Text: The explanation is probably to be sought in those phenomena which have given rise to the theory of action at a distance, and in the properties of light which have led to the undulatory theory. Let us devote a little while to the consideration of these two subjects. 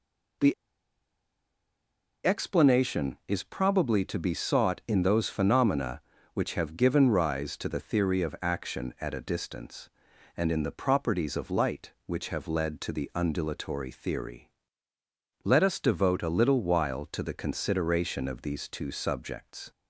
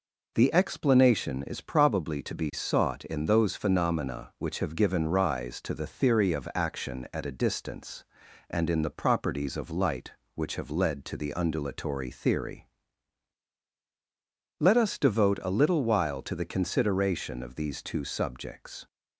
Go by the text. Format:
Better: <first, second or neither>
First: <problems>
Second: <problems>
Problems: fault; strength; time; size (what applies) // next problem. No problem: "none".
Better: second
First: pauses between "The" and "explanation"; strong; at 0.5 s; 1.7 s long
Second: none